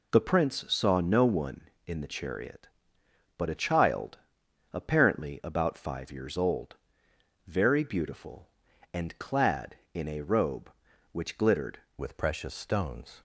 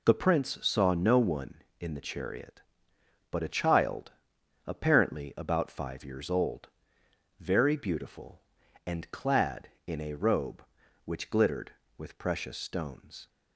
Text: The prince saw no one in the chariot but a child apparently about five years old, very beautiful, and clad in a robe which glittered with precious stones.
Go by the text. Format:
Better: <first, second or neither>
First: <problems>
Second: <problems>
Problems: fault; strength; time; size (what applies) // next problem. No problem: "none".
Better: second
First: pauses between "child" and "apparently"; noticeable; at 4.1 s; 0.54 s long // changes voice at "with"; from 11.9 s on; 1.3 s long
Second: pauses between "child" and "apparently"; noticeable; at 4.1 s; 0.54 s long